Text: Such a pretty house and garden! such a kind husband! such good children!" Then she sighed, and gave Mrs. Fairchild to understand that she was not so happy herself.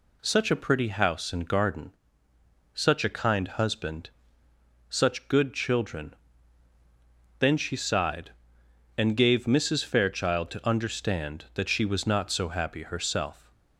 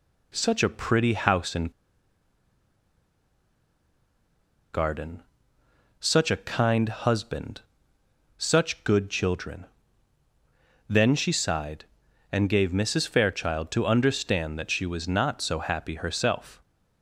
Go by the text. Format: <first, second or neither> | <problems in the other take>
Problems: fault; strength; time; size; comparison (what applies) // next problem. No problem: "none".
first | pauses between "and" and "garden"; strong; at 1.7 s; 3.0 s long